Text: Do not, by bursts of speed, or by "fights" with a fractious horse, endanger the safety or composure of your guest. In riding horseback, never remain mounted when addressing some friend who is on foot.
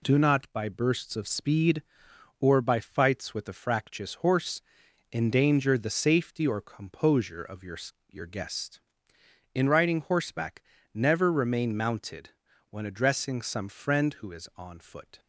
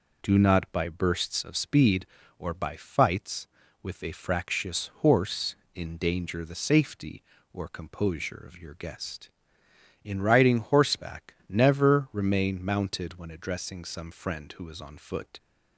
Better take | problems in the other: second | says "your" twice; at 8.1 s // pauses between "mounted" and "when"; at 12.3 s; 0.38 s long

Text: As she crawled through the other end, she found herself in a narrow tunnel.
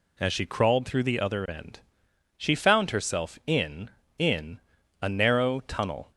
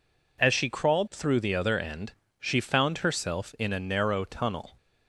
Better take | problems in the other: second | says "in" twice; at 4.1 s

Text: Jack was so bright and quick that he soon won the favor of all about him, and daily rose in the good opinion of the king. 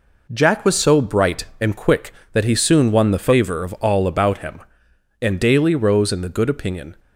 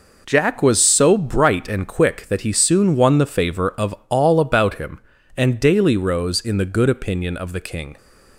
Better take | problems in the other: second | stops before "of the king"; at 6.9 s

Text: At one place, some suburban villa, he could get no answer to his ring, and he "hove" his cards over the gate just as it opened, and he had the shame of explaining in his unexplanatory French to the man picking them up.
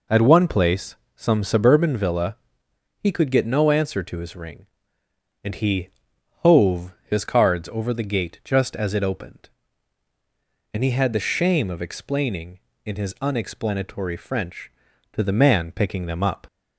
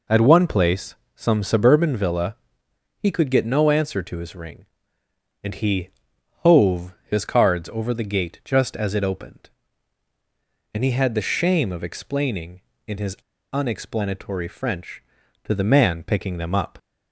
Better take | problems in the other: first | pauses between "he" and "hove"; noticeable; at 5.8 s; 0.54 s long; noticeable in the first // pauses between "hove" and "his"; slight; at 6.9 s; 0.16 s long; slight in the first // pauses between "his" and "unexplanatory"; slight; at 13.1 s; 0.35 s long

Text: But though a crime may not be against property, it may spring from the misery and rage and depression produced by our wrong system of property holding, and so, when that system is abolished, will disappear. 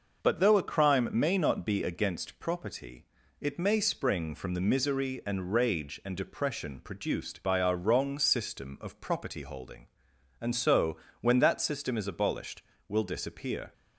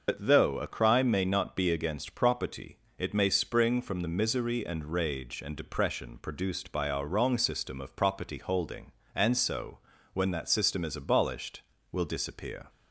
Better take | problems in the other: first | loses the start of "But"; at 0.0 s; 55 ms // starts louder than the rest; noticeable; until 1.0 s; 6 dB

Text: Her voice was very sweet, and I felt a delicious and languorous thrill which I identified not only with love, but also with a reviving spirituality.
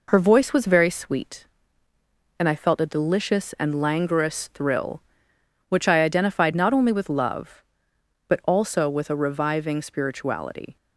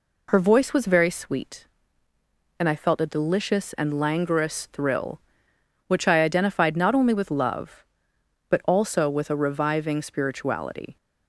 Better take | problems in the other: second | gets quieter; throughout; 3.5 dB

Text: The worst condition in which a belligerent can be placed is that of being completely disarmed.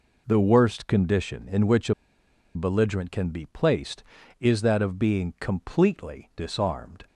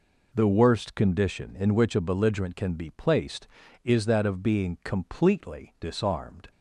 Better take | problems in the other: second | pauses between "a" and "belligerent"; noticeable; at 1.9 s; 0.61 s long

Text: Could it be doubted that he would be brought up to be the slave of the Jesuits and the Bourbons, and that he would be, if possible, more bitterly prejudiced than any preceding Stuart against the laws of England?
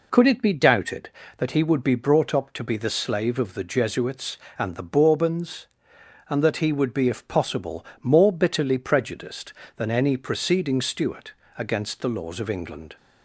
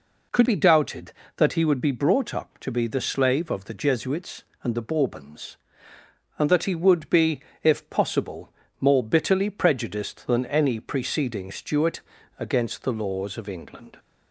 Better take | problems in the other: first | skips "it"; at 0.4 s // pauses between "Stuart" and "against"; at 11.9 s; 0.38 s long; slight in the first

